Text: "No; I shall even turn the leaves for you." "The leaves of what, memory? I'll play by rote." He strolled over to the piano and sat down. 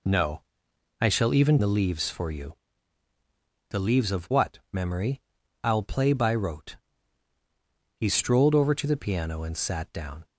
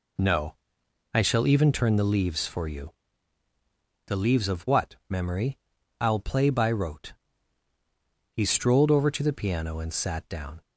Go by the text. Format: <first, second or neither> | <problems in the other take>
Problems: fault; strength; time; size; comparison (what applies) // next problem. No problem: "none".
second | skips "turn"; at 1.5 s